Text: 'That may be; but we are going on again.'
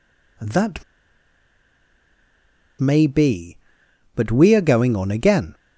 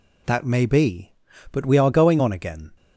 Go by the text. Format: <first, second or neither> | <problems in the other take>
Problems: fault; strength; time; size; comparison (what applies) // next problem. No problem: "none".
second | pauses between "That" and "may"; strong; at 0.8 s; 1.9 s long